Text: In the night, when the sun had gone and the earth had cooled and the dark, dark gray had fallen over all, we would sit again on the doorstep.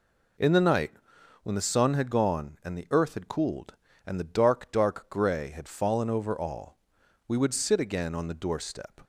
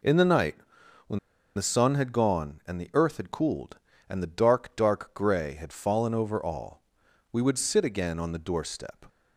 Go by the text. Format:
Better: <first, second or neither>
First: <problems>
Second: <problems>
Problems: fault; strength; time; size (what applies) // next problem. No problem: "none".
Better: first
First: none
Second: pauses between "when" and "the"; at 1.1 s; 0.36 s long